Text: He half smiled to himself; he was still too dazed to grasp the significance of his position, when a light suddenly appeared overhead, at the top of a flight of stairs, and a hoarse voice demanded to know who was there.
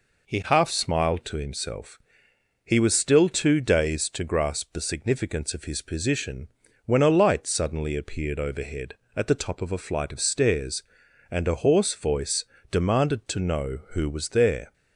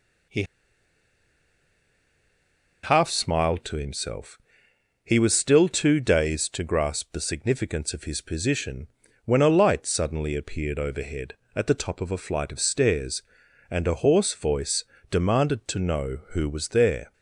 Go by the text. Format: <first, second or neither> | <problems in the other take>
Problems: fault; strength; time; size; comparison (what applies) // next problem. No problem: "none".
first | pauses between "He" and "half"; strong; at 0.4 s; 2.4 s long // pauses between "voice" and "demanded"; slight; at 14.8 s; 0.28 s long; slight in the first